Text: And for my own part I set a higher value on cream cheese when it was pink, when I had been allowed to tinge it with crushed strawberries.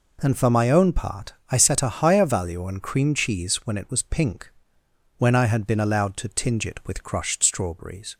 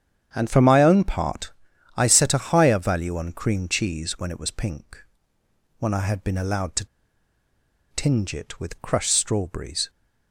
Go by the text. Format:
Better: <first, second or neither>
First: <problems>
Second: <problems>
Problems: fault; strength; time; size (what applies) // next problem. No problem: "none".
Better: first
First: pauses between "part" and "I"; slight; at 1.3 s; 0.18 s long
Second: starts louder than the rest; strong; until 1.3 s; 9 dB // pauses between "part" and "I"; noticeable; at 1.5 s; 0.46 s long // pauses between "to" and "tinge"; at 6.8 s; 1.0 s long